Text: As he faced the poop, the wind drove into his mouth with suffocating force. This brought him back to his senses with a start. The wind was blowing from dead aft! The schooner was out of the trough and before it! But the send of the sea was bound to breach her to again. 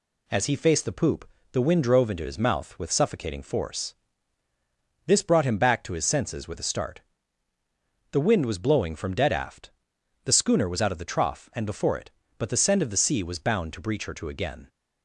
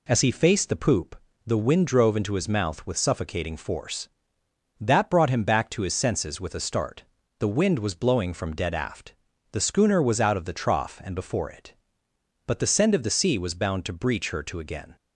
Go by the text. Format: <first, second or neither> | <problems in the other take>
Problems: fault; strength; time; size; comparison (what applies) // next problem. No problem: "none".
first | says "That" for "This"; at 4.7 s